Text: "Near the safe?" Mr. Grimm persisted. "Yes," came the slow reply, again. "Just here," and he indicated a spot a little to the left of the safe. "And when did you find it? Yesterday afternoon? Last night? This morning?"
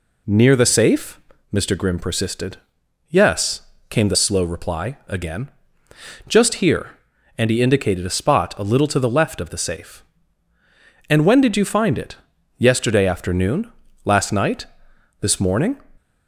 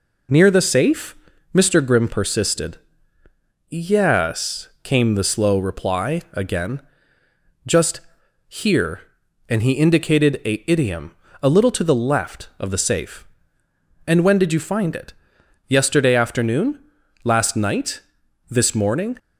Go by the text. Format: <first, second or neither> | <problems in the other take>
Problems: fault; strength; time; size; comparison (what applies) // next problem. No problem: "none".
first | pauses between "Just" and "here"; noticeable; at 7.9 s; 0.48 s long // says "idiom" for "spot"; at 10.6 s